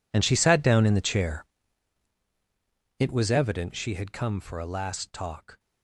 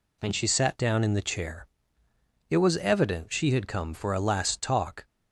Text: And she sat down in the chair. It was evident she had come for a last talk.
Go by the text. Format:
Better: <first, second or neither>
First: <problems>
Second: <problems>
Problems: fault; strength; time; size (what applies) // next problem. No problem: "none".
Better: second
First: gets quieter; strong; throughout; 18.5 dB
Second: none